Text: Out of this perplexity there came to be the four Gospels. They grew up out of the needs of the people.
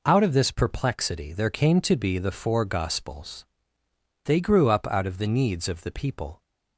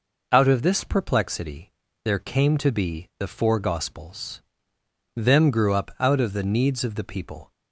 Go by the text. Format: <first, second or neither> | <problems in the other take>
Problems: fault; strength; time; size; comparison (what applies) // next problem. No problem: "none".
first | pauses between "perplexity" and "there"; slight; at 1.7 s; 0.32 s long // says "Them" for "They"; at 5.1 s